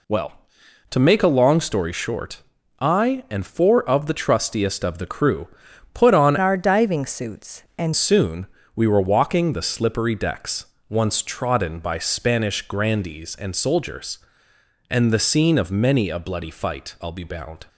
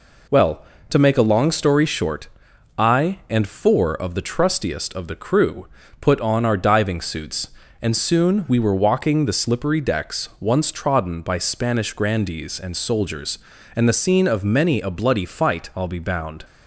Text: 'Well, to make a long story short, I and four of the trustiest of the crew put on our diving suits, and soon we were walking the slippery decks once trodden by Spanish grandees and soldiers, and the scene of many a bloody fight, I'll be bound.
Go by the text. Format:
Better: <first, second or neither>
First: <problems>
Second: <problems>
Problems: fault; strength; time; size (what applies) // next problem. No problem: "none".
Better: second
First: pauses between "crew" and "put"; noticeable; at 5.4 s; 0.46 s long // changes voice from "our" to "and"; from 6.3 to 7.9 s; 1.6 s long // pauses between "soon" and "we"; slight; at 8.4 s; 0.30 s long // pauses between "decks" and "once"; slight; at 10.6 s; 0.24 s long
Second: pauses between "crew" and "put"; slight; at 5.6 s; 0.34 s long